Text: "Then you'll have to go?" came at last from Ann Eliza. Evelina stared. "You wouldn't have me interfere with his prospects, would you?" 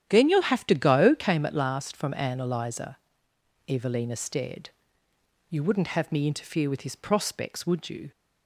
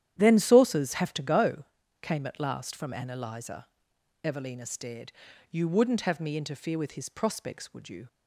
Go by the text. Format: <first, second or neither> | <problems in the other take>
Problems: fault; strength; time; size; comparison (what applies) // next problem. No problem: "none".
first | starts louder than the rest; strong; until 1.1 s; 11 dB; strong in the first // says "saucers" for "you'll"; at 0.3 s